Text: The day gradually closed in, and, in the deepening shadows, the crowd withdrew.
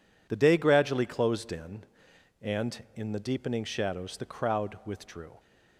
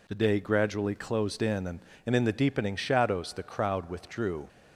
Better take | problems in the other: first | says "and" twice; at 2.0 s

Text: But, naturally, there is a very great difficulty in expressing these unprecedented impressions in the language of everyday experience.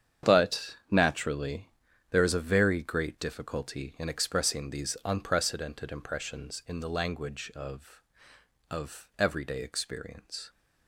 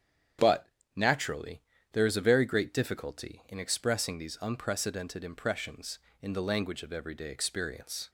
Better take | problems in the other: second | starts louder than the rest; strong; until 1.3 s; 8.5 dB; strong in the second // says "of" twice; at 8.7 s

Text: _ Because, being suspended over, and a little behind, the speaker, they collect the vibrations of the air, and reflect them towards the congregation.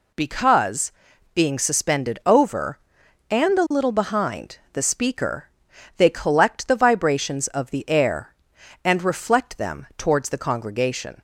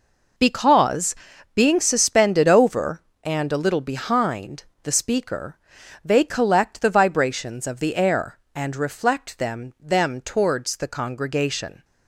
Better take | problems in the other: first | says "them" twice; at 9.8 s

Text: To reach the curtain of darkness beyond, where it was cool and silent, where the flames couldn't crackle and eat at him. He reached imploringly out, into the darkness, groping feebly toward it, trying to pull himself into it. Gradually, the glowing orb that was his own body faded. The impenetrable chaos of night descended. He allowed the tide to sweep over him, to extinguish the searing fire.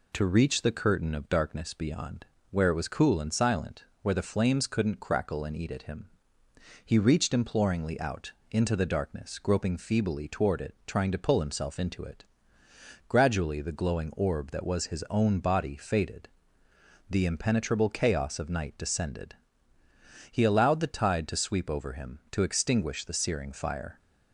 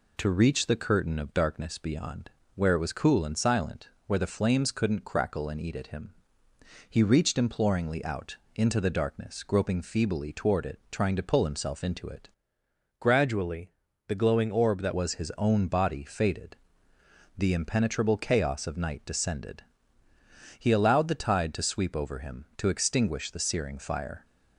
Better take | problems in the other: first | changes voice from "Gradually" to "that"; from 12.9 to 14.9 s; 2.0 s long

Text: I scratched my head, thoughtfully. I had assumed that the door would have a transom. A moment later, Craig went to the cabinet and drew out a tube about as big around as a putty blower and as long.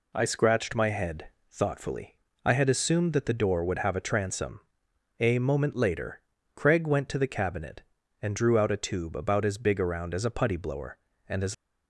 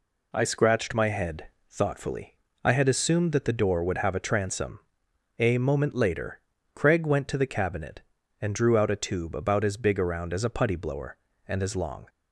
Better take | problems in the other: second | stops before "long"; at 11.5 s

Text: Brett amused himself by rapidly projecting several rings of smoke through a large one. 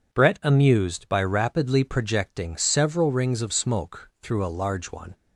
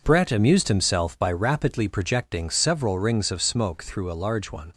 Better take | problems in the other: second | skips "himself"; at 1.0 s

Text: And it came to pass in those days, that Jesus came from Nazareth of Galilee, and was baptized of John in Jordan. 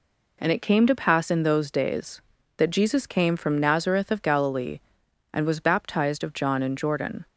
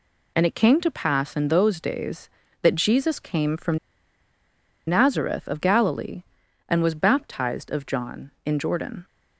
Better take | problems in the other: first | pauses between "from" and "Nazareth"; at 3.7 s; 1.1 s long

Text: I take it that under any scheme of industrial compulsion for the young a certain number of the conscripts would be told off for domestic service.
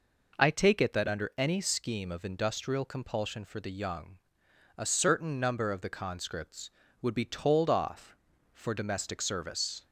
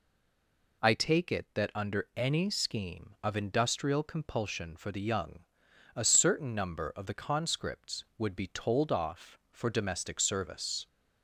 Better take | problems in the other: first | stays silent before the first word; slight; until 0.8 s; 0.8 s long // pauses between "young" and "a"; noticeable; at 5.3 s; 0.58 s long; noticeable in the first

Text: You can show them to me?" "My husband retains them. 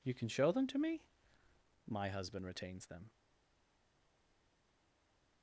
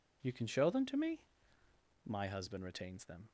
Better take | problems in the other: second | stays silent after the last word; from 3.0 s on; 2.4 s long

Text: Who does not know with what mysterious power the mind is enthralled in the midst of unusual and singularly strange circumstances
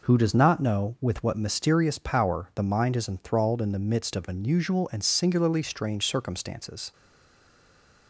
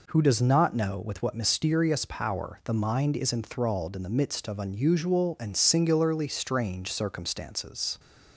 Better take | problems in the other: second | stays silent after the last word; noticeable; from 6.9 s on; 1.1 s long

